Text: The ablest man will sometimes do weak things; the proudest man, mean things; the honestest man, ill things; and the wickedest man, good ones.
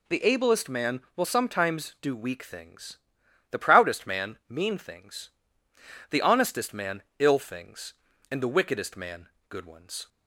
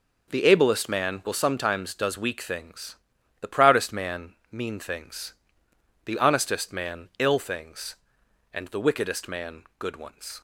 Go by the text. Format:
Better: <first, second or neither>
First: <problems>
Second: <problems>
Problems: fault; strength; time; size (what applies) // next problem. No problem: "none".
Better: first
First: none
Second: says "does" for "do"; at 1.9 s